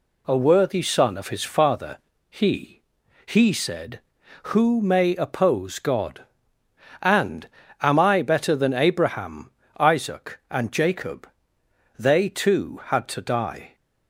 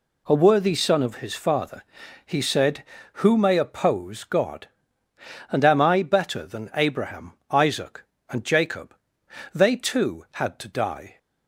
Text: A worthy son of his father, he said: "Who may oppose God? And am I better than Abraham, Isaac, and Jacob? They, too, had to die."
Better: second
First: says "he" twice; at 3.2 s // pauses between "And" and "am"; slight; at 7.4 s; 0.36 s long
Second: none

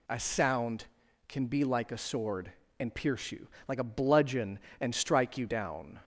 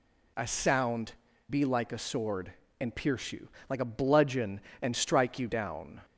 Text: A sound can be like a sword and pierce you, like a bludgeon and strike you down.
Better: first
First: none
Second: skips "can"; at 1.3 s

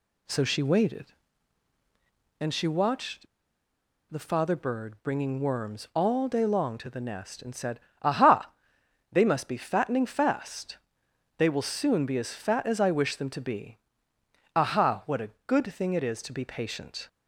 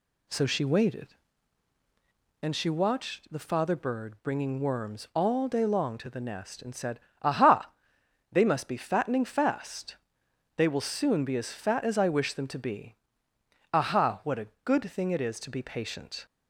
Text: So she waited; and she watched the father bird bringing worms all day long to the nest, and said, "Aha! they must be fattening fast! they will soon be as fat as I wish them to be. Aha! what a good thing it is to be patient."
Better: second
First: pauses between "watched" and "the"; noticeable; at 3.2 s; 0.84 s long // pauses between "a" and "good"; slight; at 15.2 s; 0.16 s long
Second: pauses between "a" and "good"; slight; at 14.4 s; 0.16 s long

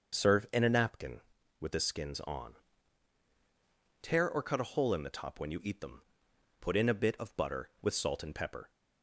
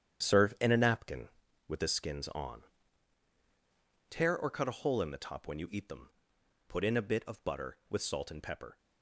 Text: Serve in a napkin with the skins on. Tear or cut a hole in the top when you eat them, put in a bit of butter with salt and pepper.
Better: first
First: starts louder than the rest; until 1.2 s; 6 dB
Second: gets quieter; strong; throughout; 10 dB // starts louder than the rest; strong; until 1.3 s; 9 dB

